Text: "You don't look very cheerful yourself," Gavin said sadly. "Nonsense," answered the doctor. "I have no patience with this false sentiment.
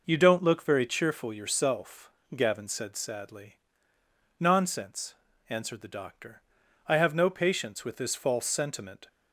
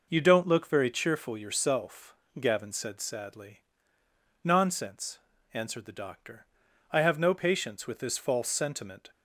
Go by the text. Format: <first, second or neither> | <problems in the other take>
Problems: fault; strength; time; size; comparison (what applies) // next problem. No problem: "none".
neither | none